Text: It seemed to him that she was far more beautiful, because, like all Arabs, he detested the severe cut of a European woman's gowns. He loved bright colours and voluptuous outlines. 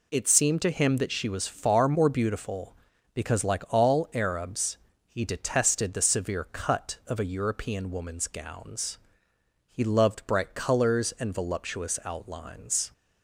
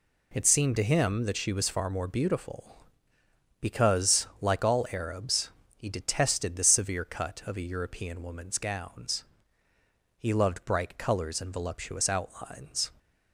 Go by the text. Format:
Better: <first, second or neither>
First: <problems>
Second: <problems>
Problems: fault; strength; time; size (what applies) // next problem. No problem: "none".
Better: neither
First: none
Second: none